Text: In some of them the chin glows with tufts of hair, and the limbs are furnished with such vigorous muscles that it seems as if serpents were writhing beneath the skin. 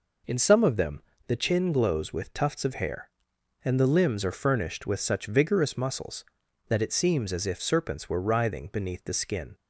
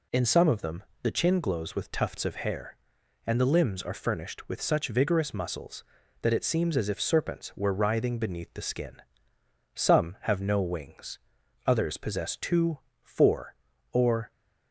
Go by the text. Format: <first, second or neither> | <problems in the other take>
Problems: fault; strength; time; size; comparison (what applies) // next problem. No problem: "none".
first | pauses between "them" and "the"; slight; at 0.8 s; 0.20 s long; slight in the first // goes on to say "Some have no wings others possess two four or"; strong; from 9.7 s on; 4.5 s long